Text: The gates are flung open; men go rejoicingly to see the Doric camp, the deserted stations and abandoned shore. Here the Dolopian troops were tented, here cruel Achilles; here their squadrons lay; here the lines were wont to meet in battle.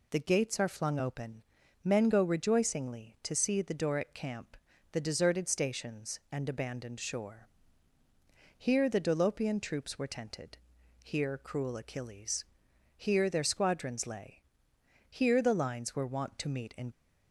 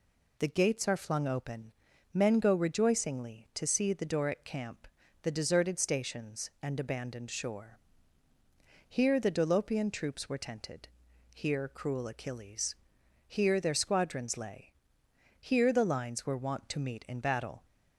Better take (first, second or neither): second